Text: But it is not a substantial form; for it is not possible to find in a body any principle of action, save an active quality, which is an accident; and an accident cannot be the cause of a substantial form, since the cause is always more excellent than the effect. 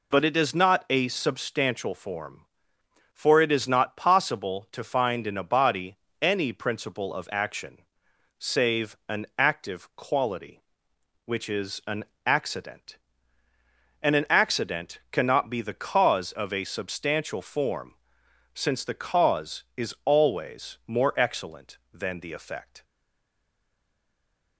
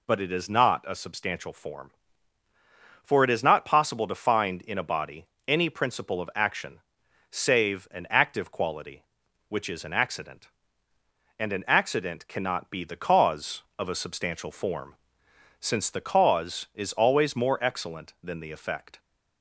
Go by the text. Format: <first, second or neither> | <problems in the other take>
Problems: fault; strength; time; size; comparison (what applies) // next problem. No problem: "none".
second | pauses between "body" and "any"; slight; at 5.9 s; 0.24 s long; slight in the second // pauses between "an" and "accident"; slight; at 12.0 s; 0.22 s long // stays silent after the last word; noticeable; from 22.8 s on; 1.7 s long